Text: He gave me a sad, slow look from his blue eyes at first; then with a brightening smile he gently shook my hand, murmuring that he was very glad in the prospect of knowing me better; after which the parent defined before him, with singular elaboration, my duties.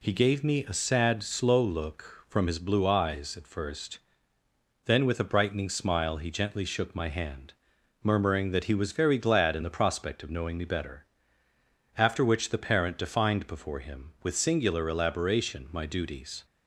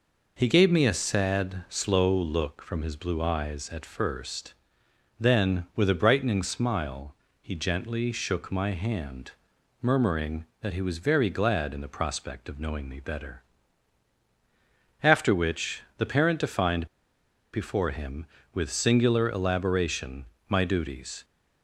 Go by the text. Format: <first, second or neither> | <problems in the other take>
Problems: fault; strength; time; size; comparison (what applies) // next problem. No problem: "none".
first | pauses between "smile" and "he"; slight; at 7.1 s; 0.26 s long // pauses between "which" and "the"; slight; at 15.8 s; 0.16 s long // pauses between "defined" and "before"; noticeable; at 16.8 s; 0.67 s long